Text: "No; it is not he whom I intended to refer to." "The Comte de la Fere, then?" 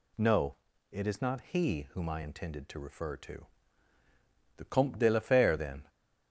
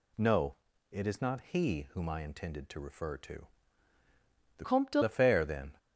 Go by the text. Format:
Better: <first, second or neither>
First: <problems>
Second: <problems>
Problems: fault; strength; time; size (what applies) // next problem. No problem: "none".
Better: first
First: none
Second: changes voice from "Comte" to "de"; from 4.6 to 5.0 s; 0.4 s long